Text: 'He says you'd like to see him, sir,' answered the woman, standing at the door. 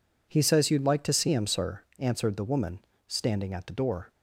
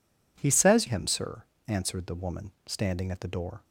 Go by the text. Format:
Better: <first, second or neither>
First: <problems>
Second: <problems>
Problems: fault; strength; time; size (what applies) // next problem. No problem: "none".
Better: first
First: none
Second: skips "you'd like to see"; at 0.8 s